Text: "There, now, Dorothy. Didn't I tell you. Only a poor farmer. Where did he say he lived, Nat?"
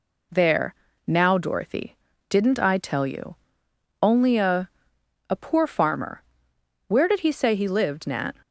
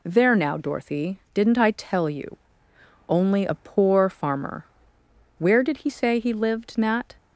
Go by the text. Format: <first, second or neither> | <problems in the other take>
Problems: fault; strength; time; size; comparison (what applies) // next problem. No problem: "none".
second | says "a" twice; at 5.2 s